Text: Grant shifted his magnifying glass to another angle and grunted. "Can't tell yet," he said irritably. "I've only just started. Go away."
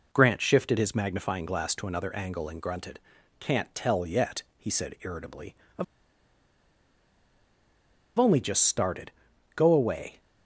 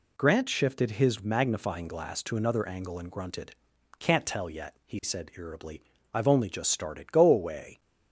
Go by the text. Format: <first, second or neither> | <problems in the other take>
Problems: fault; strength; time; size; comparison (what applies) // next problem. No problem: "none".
second | pauses between "I've" and "only"; strong; at 5.8 s; 2.3 s long